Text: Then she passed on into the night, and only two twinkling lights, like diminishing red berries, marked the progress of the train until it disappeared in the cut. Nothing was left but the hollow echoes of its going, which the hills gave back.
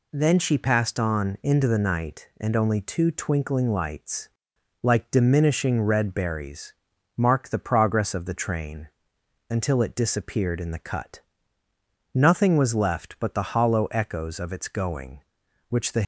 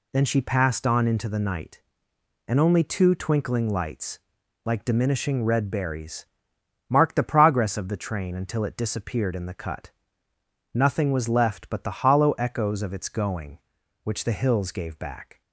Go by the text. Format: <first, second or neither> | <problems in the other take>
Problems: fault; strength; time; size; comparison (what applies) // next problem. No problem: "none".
second | pauses between "train" and "until"; noticeable; at 8.8 s; 0.62 s long // stops before "hills gave back"; at 16.0 s